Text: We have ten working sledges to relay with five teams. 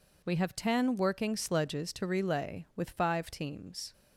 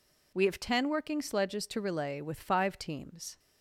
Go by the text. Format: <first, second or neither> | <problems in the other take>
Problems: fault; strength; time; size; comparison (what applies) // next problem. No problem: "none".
neither | none